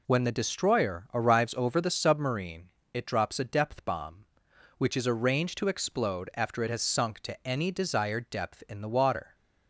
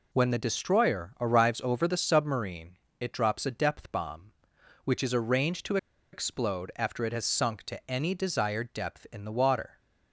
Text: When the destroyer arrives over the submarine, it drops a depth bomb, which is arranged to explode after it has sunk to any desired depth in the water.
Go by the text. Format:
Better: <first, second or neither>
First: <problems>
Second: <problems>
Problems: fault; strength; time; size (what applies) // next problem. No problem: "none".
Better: first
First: none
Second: pauses between "to" and "explode"; at 5.7 s; 0.36 s long